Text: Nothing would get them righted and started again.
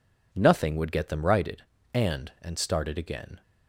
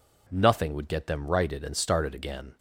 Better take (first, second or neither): second